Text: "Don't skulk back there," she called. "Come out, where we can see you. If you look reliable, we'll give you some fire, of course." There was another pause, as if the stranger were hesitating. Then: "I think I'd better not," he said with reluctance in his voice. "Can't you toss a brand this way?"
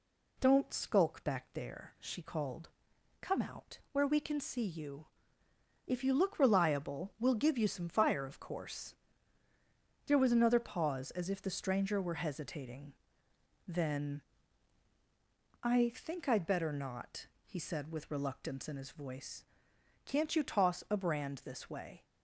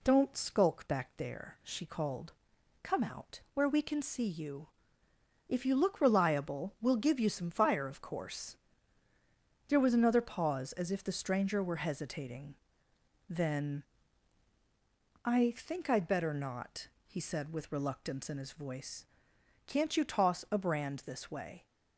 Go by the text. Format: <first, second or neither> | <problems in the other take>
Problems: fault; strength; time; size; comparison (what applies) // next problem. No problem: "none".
neither | none